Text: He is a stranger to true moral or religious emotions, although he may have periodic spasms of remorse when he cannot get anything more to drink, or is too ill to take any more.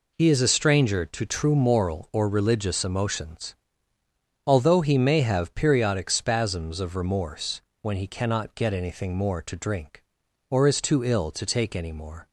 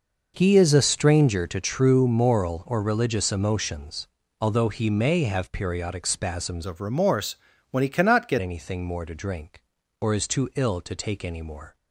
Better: first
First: pauses between "remorse" and "when"; slight; at 7.6 s; 0.20 s long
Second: changes voice from "of" to "get"; from 6.6 to 8.3 s; 1.7 s long // pauses between "remorse" and "when"; slight; at 7.3 s; 0.36 s long

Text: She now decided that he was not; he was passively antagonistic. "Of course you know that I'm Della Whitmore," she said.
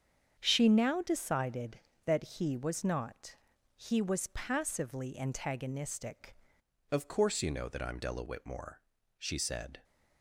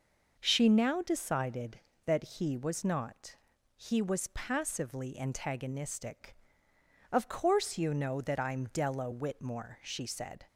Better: second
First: starts louder than the rest; strong; until 1.3 s; 7.5 dB // changes voice at "Of"; from 6.8 s on; 3.0 s long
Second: none

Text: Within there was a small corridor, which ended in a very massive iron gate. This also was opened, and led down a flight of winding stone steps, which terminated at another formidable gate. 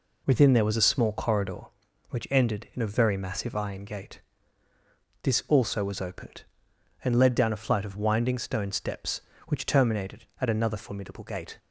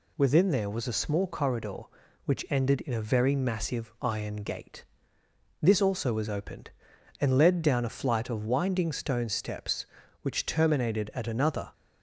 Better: first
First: none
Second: stops before "formidable gate"; at 11.7 s

